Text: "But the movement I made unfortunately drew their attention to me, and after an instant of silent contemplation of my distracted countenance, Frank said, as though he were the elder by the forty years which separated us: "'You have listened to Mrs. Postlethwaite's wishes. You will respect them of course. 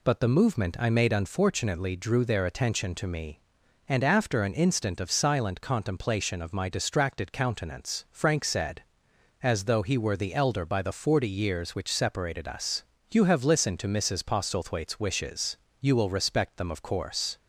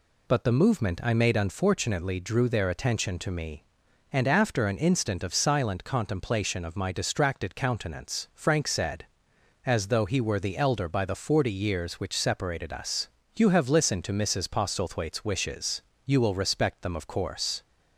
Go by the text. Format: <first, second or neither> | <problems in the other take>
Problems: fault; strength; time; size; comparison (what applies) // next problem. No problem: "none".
neither | none